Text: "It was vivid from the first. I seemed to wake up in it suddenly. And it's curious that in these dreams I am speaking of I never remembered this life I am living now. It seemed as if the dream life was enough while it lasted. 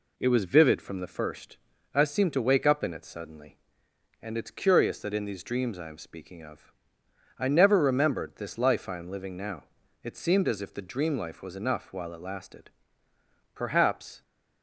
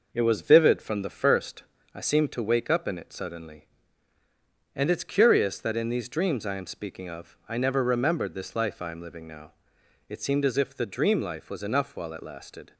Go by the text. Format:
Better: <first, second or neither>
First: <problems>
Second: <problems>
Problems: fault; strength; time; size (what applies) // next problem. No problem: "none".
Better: second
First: pauses between "of" and "I"; noticeable; at 6.7 s; 0.66 s long // goes on to say "Perhaps"; noticeable; from 13.5 s on; 0.68 s long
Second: none